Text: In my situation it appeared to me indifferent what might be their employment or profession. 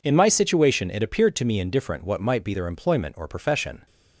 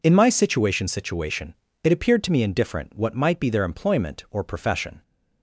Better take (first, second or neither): first